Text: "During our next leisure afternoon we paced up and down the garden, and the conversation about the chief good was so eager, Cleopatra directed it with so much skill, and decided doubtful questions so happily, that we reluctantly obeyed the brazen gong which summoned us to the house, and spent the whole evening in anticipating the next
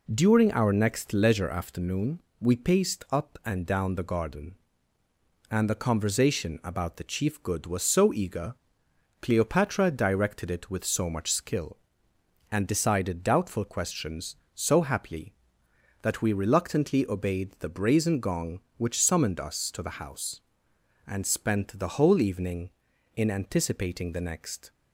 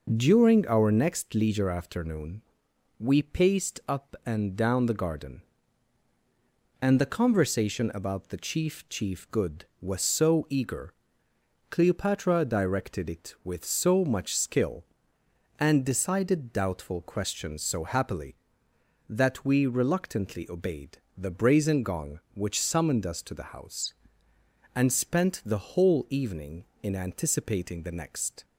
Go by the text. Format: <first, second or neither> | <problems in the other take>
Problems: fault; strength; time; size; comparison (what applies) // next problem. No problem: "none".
first | pauses between "afternoon" and "we"; noticeable; at 2.4 s; 0.58 s long; slight in the first // says "chief" twice; at 8.8 s // pauses between "obeyed" and "the"; slight; at 20.9 s; 0.22 s long